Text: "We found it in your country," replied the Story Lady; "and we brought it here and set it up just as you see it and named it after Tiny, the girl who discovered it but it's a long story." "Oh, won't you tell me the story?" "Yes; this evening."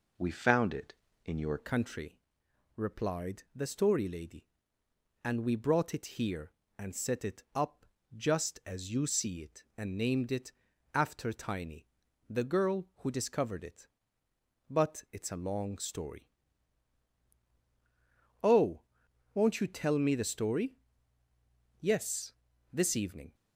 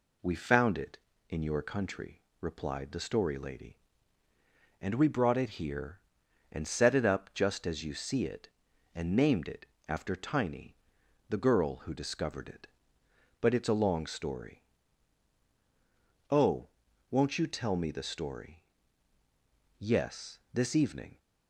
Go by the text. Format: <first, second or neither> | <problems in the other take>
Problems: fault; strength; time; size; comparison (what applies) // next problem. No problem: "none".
second | changes voice at "country"; from 1.5 s on; 21.8 s long // pauses between "up" and "just"; slight; at 7.8 s; 0.30 s long // pauses between "it" and "after"; at 10.4 s; 0.42 s long; slight in the second